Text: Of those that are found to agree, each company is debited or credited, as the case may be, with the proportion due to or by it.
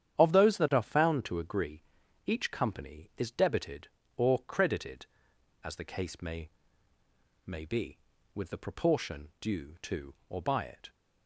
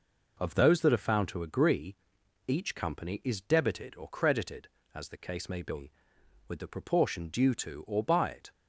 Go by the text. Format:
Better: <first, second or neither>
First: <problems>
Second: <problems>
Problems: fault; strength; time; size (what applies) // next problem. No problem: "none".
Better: second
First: starts louder than the rest; strong; until 1.2 s; 9.5 dB // says "may" twice; at 7.4 s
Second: none